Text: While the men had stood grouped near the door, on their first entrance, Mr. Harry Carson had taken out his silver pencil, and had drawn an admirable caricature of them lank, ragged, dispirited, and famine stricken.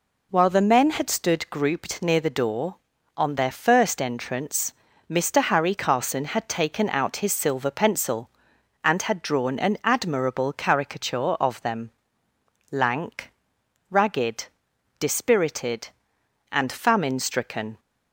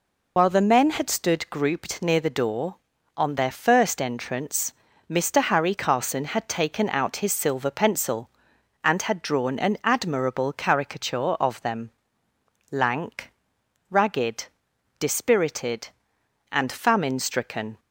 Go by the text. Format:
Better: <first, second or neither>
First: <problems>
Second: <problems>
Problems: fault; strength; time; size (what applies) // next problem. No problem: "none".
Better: first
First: pauses between "them" and "lank"; noticeable; at 11.8 s; 0.82 s long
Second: loses the start of "While"; at 0.3 s; 50 ms // pauses between "them" and "lank"; noticeable; at 11.8 s; 0.82 s long